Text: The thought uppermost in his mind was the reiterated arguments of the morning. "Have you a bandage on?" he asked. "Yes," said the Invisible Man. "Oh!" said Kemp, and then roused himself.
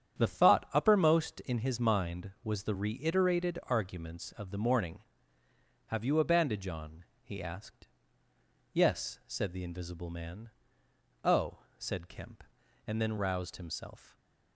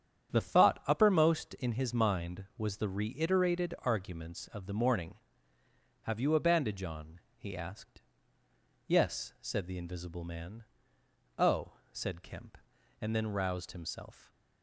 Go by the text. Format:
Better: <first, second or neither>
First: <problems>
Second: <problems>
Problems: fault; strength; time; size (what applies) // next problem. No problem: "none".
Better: neither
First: starts louder than the rest; strong; until 1.2 s; 9 dB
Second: starts louder than the rest; strong; until 1.4 s; 9 dB